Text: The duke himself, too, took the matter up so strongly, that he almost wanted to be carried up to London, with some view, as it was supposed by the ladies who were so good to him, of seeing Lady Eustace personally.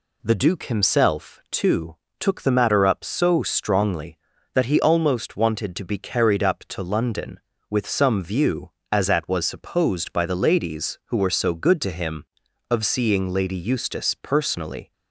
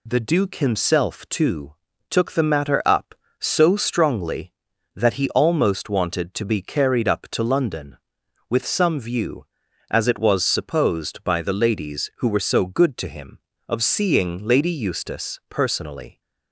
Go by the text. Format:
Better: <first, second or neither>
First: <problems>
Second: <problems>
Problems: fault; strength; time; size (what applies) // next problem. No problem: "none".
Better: second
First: says "at" for "it"; at 9.0 s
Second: none